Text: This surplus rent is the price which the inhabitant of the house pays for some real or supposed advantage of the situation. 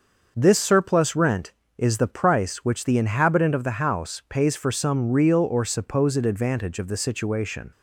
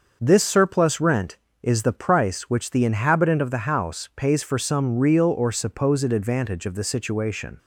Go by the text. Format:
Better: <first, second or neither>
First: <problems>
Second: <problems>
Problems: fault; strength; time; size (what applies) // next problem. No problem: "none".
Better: neither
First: starts louder than the rest; until 1.3 s; 6 dB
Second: starts louder than the rest; until 1.2 s; 6 dB